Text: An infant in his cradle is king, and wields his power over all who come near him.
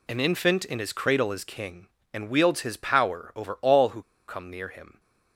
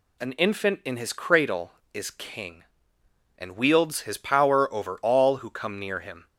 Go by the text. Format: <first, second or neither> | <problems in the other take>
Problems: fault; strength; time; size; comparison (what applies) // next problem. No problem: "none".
second | pauses between "who" and "come"; slight; at 4.0 s; 0.25 s long